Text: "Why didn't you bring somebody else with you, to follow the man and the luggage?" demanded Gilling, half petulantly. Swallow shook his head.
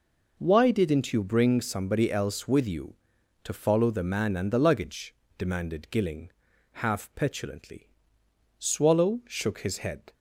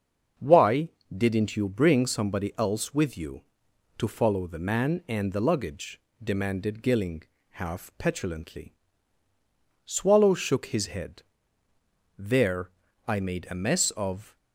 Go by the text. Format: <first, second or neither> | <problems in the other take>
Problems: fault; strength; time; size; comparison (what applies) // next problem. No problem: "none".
first | starts louder than the rest; until 1.6 s; 6.5 dB // pauses between "Why" and "didn't"; slight; at 0.8 s; 0.26 s long // goes on to say "There I made a mess of"; strong; from 12.1 s on; 2.1 s long